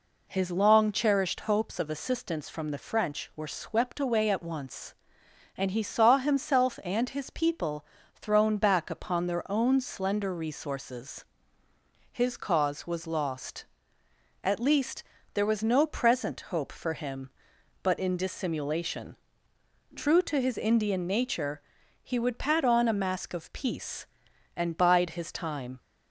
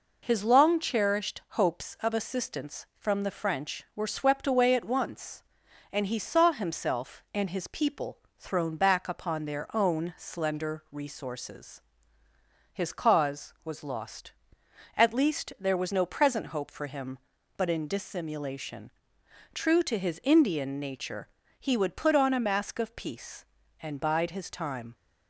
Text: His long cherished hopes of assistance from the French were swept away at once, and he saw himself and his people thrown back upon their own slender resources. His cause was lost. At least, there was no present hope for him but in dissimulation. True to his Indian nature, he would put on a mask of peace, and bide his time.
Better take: second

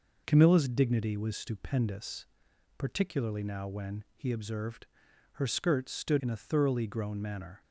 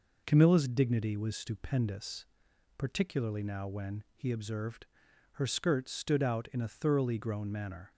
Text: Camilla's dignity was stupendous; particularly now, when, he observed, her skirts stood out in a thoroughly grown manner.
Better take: second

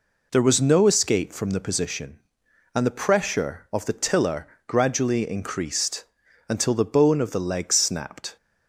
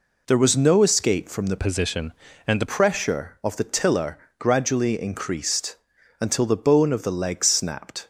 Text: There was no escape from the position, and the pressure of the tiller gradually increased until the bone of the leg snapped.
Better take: first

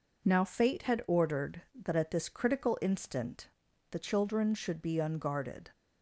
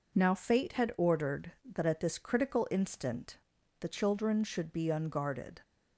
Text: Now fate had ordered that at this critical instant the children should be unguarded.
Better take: neither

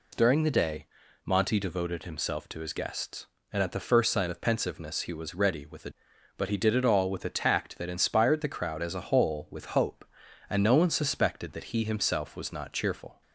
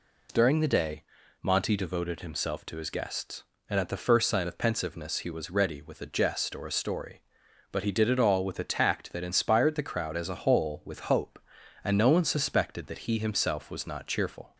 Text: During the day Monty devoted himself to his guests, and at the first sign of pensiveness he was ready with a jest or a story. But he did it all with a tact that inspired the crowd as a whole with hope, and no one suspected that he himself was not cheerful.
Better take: second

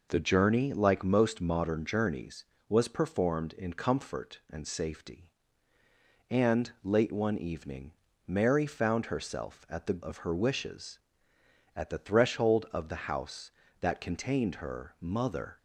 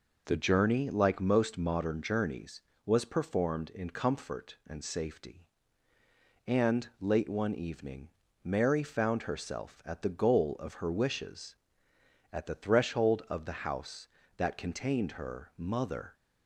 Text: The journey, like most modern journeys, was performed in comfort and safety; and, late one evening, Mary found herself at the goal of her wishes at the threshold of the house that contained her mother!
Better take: second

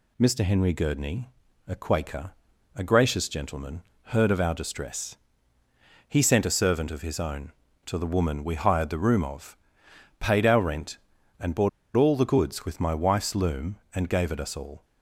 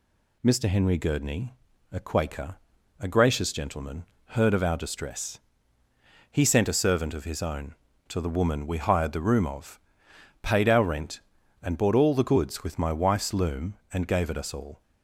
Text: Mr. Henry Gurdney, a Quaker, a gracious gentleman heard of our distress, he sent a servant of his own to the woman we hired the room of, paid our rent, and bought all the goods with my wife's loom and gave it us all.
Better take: second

